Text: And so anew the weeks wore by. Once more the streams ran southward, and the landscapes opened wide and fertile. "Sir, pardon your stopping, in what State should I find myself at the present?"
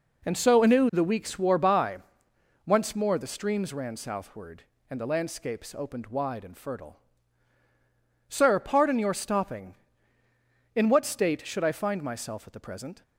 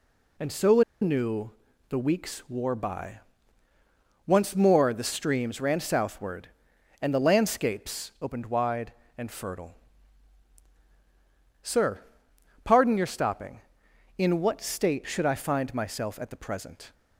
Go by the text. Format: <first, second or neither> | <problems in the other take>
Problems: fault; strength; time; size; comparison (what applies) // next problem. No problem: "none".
first | pauses between "so" and "anew"; slight; at 0.8 s; 0.20 s long // pauses between "anew" and "the"; at 1.5 s; 0.38 s long